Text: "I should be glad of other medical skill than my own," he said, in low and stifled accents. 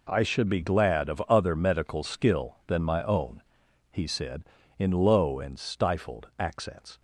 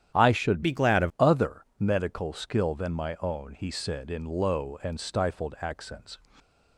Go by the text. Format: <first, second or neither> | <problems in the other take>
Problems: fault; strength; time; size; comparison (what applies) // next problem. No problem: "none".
first | starts louder than the rest; strong; until 1.2 s; 10 dB // changes voice from "be" to "of"; from 0.6 to 1.1 s; 0.5 s long